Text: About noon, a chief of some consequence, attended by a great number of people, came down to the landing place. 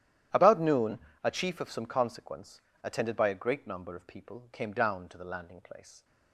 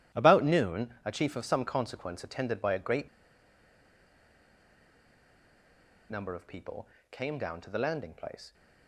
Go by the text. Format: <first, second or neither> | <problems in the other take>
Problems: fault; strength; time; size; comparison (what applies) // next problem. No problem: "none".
first | starts louder than the rest; strong; until 1.2 s; 12.5 dB; strong in the first // pauses between "great" and "number"; strong; at 3.0 s; 3.0 s long